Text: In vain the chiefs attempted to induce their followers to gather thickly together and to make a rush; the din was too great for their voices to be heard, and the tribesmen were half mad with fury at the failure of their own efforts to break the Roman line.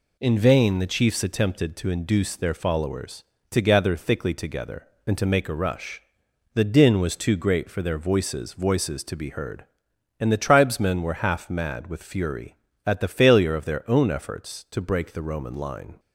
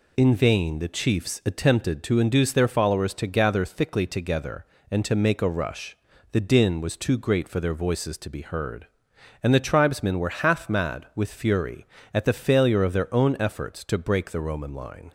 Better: second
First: says "voices" twice; at 8.5 s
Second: none

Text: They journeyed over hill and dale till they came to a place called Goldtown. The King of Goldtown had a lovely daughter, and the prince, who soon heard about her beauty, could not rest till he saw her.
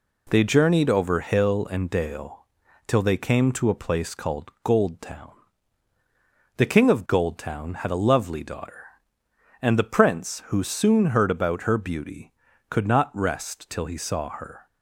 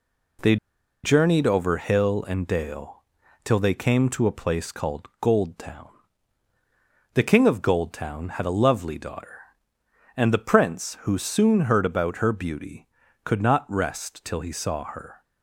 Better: first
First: pauses between "dale" and "till"; at 2.4 s; 0.40 s long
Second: pauses between "They" and "journeyed"; noticeable; at 0.5 s; 0.47 s long // pauses between "dale" and "till"; at 3.0 s; 0.40 s long

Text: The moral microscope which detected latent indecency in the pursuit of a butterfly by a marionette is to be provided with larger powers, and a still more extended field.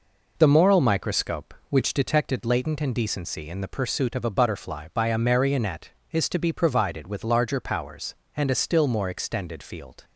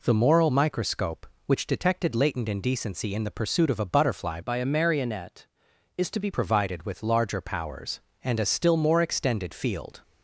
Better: first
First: none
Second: changes voice from "by" to "be"; from 4.4 to 6.2 s; 1.8 s long

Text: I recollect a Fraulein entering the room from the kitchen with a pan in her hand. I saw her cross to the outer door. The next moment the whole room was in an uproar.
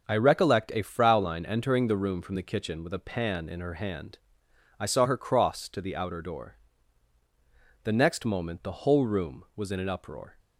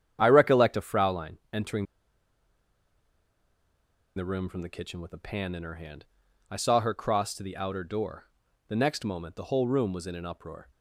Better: first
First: starts louder than the rest; until 1.1 s; 6.5 dB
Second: starts louder than the rest; strong; until 1.2 s; 9 dB // pauses between "entering" and "the"; strong; at 1.8 s; 2.3 s long

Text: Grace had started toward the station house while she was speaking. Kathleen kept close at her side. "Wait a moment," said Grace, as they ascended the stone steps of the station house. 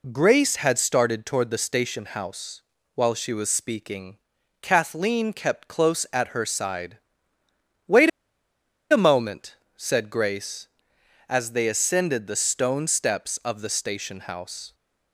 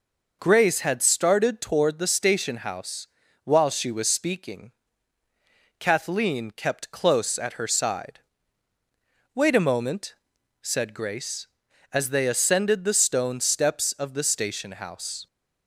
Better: second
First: pauses between "house" and "while"; slight; at 2.6 s; 0.32 s long // pauses between "Wait" and "a"; noticeable; at 8.0 s; 0.82 s long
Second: pauses between "house" and "while"; slight; at 3.0 s; 0.36 s long

